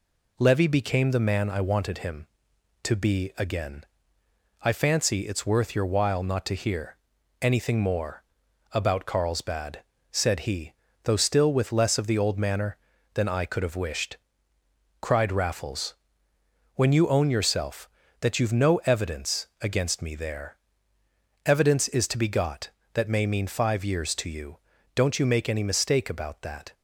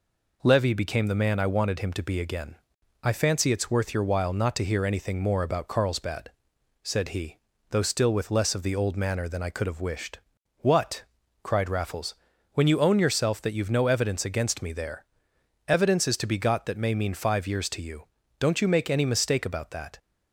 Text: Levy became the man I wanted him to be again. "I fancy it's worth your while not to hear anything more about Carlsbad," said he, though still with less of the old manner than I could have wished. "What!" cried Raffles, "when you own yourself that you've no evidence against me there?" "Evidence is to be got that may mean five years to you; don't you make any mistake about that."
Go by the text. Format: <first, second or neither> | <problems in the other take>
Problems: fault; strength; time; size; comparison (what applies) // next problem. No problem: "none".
second | pauses between "hear" and "anything"; at 6.9 s; 0.44 s long // pauses between "more" and "about"; noticeable; at 8.2 s; 0.50 s long // skips "What"; at 14.5 s